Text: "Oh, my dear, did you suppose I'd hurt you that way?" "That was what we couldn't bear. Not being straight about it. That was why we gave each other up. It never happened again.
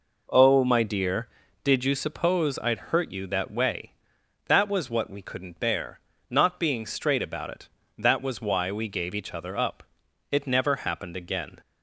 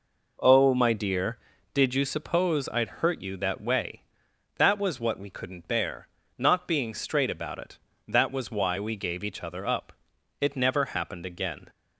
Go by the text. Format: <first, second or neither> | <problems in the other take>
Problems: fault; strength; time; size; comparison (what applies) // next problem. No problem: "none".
neither | none